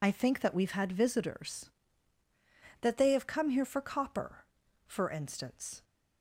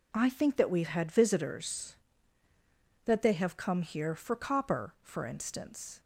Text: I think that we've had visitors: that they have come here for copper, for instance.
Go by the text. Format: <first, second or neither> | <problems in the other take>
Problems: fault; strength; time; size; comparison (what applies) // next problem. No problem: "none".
second | loses the start of "I"; at 0.0 s; 45 ms